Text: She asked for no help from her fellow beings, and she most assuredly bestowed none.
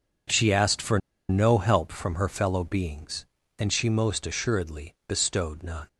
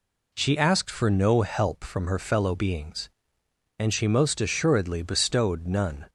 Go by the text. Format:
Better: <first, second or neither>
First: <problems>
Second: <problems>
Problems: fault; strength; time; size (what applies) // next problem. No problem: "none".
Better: second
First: pauses between "for" and "no"; slight; at 0.9 s; 0.30 s long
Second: none